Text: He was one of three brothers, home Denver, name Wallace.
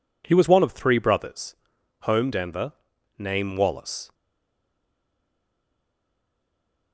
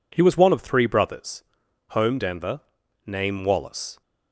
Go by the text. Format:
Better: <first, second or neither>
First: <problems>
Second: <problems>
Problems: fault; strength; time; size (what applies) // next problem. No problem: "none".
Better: second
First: stays silent after the last word; strong; from 4.1 s on; 2.8 s long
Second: none